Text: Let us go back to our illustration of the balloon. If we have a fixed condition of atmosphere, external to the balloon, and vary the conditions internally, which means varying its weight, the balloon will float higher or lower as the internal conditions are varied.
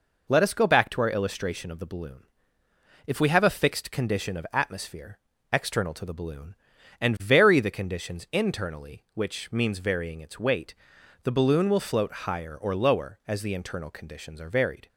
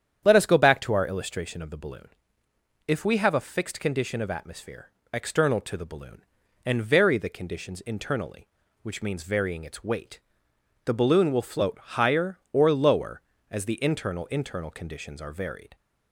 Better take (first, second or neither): first